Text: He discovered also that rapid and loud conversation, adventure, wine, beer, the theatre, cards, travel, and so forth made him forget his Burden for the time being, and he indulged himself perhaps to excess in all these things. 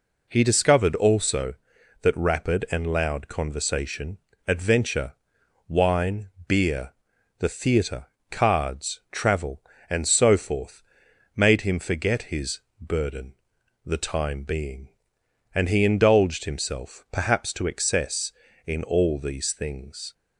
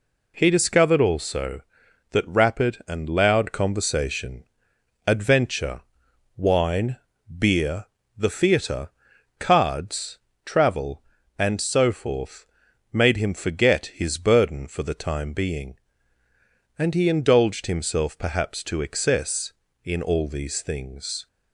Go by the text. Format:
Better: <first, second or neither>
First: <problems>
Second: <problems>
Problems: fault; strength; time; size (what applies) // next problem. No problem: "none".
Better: second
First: pauses between "forth" and "made"; noticeable; at 10.8 s; 0.52 s long // pauses between "his" and "Burden"; slight; at 12.6 s; 0.20 s long // skips "for"; at 13.5 s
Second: pauses between "forth" and "made"; noticeable; at 12.4 s; 0.46 s long